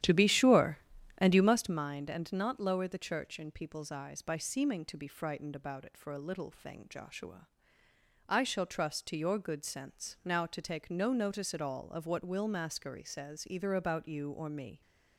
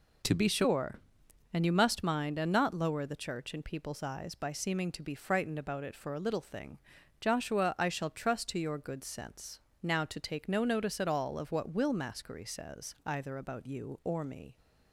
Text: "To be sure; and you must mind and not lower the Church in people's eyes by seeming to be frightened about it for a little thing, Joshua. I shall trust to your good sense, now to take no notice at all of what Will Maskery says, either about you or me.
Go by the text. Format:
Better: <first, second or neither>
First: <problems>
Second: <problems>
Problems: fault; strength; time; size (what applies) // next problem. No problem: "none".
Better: second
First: starts louder than the rest; strong; until 1.8 s; 11.5 dB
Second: none